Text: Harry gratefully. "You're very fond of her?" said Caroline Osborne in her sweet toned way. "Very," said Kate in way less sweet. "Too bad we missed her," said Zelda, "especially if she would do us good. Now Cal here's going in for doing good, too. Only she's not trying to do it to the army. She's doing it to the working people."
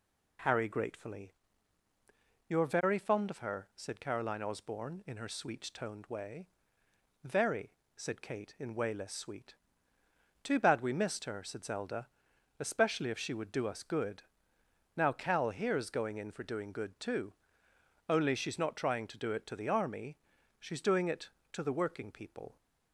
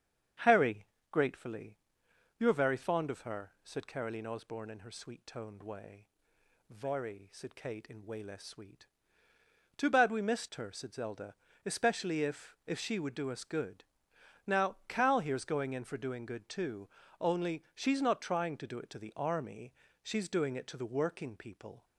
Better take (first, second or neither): first